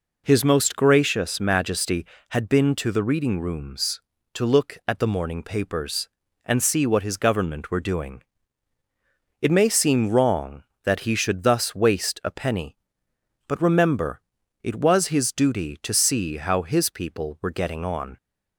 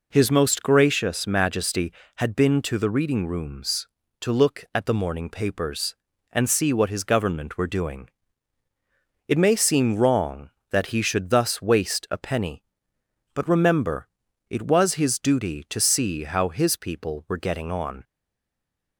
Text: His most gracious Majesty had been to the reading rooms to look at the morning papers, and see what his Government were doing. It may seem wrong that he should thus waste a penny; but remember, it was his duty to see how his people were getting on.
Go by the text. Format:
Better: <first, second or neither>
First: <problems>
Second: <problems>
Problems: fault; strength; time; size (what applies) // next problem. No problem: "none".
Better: first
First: none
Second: stays silent after the last word; slight; from 18.0 s on; 0.9 s long